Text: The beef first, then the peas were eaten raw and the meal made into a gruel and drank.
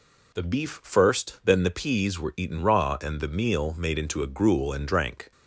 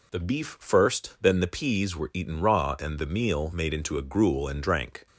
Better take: neither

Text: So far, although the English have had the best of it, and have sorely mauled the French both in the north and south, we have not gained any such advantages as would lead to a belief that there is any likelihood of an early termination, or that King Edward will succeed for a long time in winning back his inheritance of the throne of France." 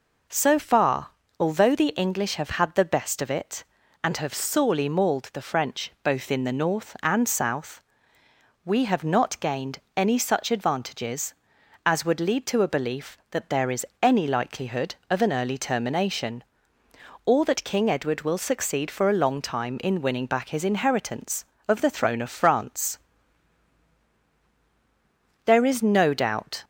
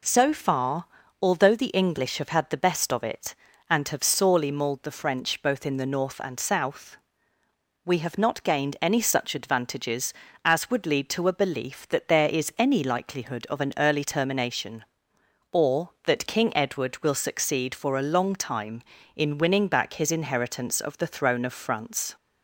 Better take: second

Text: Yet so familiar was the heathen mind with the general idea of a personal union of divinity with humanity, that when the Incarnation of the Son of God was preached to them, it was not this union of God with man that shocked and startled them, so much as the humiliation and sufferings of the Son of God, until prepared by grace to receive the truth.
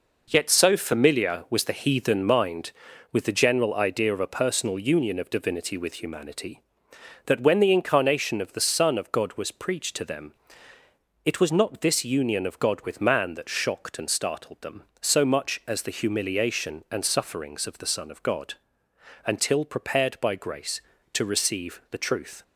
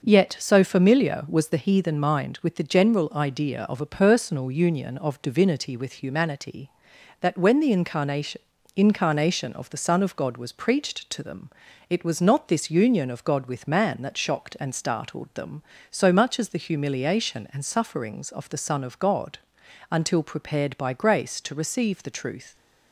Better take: first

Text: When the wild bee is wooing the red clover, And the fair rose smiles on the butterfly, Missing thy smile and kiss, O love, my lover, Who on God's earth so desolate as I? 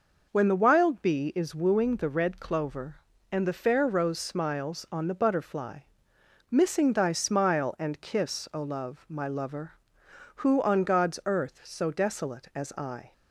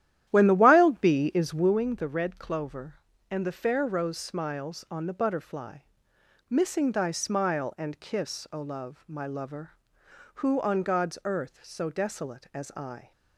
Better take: first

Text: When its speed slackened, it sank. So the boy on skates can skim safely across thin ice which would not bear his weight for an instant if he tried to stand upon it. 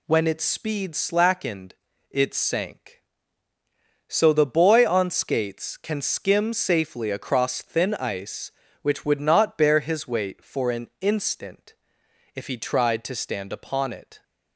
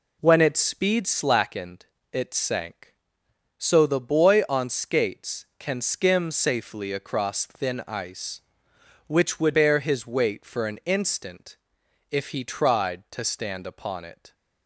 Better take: first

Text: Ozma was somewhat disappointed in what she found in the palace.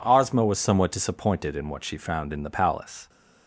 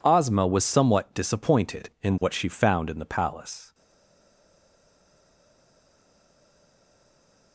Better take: first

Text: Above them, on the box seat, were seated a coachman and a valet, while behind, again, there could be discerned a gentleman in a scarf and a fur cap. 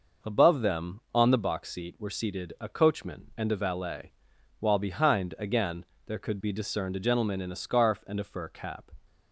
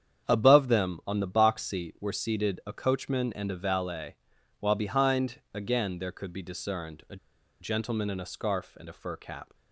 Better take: first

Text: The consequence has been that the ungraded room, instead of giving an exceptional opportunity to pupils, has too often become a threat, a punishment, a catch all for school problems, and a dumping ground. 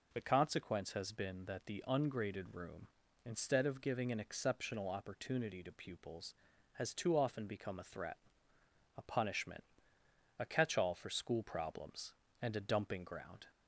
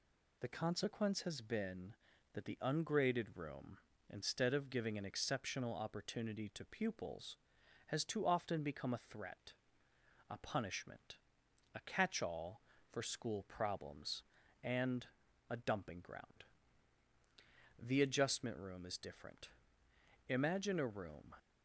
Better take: first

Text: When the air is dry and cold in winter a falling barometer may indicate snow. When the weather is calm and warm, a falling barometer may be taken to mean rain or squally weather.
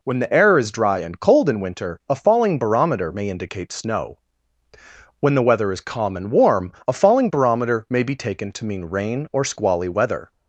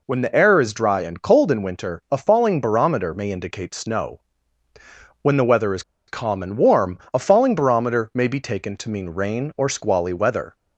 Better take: first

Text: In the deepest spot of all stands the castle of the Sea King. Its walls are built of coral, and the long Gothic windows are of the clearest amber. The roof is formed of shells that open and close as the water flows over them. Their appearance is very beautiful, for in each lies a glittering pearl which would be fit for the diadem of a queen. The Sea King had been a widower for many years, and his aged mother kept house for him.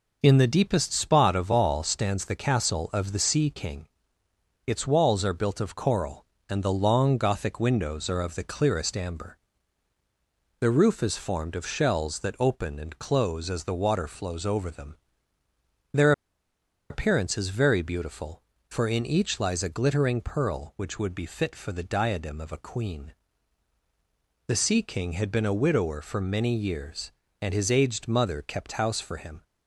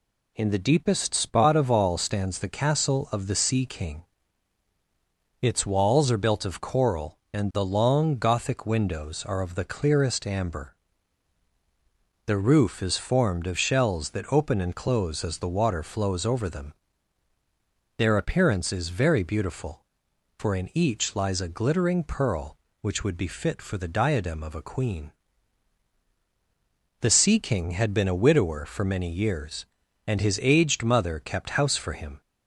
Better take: second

